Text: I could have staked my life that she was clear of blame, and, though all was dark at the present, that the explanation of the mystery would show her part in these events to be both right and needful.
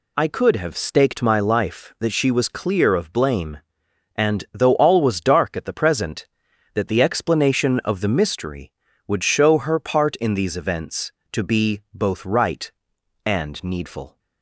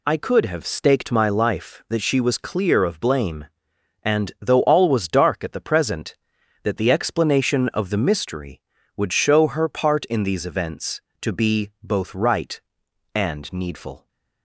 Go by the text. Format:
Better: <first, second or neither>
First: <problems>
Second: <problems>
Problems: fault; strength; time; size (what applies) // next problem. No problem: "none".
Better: neither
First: none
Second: none